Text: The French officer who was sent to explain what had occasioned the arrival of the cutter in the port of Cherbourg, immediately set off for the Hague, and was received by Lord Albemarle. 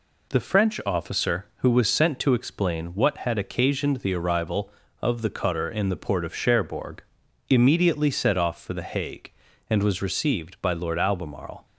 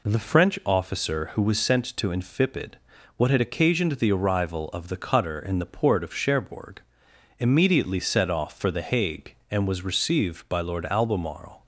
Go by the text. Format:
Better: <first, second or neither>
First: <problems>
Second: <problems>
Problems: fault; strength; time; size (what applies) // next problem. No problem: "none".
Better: first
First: none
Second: says "infipid" for "explain"; at 2.0 s